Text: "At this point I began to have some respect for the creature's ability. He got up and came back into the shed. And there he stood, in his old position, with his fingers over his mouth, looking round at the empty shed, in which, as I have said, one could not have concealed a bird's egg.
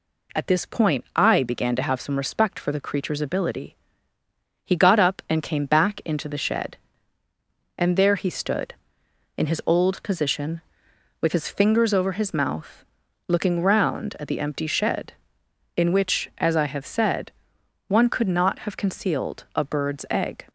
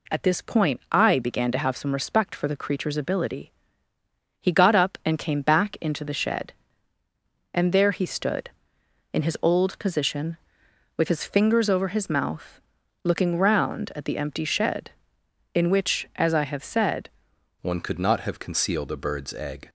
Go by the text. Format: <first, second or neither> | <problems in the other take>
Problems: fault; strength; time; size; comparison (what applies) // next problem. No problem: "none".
first | changes voice at "one"; from 17.6 s on; 2.0 s long